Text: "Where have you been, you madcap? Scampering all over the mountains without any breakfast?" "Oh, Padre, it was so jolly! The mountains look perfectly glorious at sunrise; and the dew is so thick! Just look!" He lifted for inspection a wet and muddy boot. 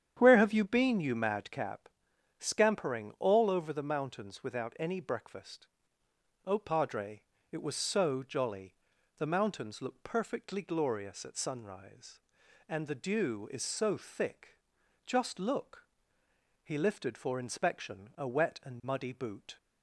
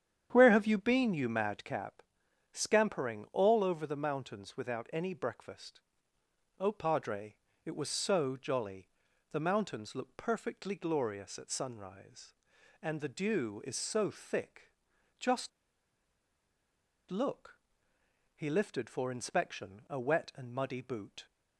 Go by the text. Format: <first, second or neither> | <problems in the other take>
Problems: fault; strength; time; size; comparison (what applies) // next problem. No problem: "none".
first | starts louder than the rest; strong; until 1.3 s; 9 dB; strong in the first // pauses between "Just" and "look"; strong; at 15.4 s; 1.5 s long